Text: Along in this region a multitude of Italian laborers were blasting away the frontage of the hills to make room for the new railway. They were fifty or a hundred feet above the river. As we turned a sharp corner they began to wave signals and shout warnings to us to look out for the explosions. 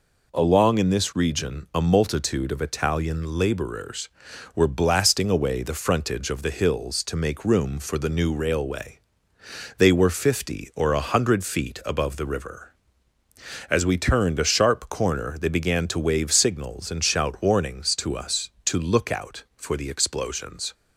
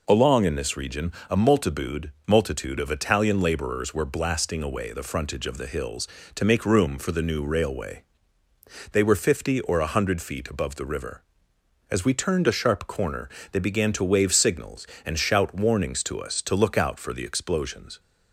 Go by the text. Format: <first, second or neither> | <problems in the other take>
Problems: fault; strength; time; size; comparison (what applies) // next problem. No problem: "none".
first | pauses between "region" and "a"; slight; at 1.1 s; 0.20 s long // says "multitude" twice; at 2.2 s // pauses between "corner" and "they"; slight; at 13.2 s; 0.22 s long